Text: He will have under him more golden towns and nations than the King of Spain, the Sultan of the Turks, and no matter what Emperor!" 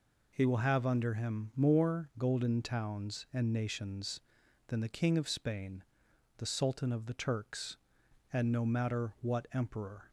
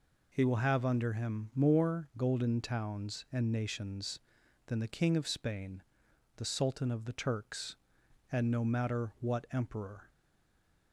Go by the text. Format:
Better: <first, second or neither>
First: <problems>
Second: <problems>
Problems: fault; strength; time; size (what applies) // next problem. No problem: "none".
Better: first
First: none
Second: stays silent after the last word; slight; from 10.0 s on; 0.9 s long